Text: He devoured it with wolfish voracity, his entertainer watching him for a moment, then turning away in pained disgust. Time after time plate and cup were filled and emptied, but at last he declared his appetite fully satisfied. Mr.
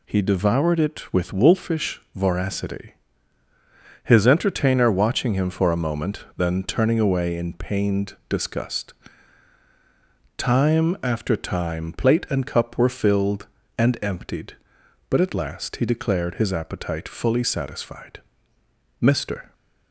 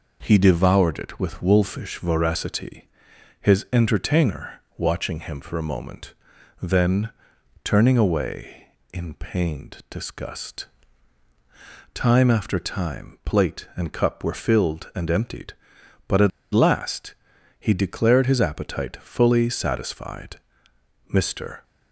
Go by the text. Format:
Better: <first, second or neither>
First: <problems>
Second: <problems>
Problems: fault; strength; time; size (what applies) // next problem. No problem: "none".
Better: first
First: none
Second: pauses between "entertainer" and "watching"; slight; at 4.6 s; 0.16 s long // pauses between "then" and "turning"; noticeable; at 7.0 s; 0.54 s long // pauses between "at" and "last"; slight; at 16.3 s; 0.22 s long // pauses between "last" and "he"; at 17.1 s; 0.44 s long